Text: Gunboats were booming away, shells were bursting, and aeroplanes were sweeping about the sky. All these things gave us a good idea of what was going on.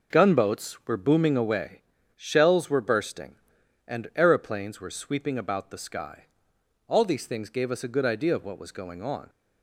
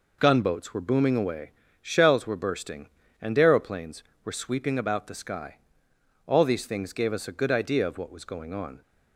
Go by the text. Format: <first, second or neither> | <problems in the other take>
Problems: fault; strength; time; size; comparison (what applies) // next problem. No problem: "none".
neither | none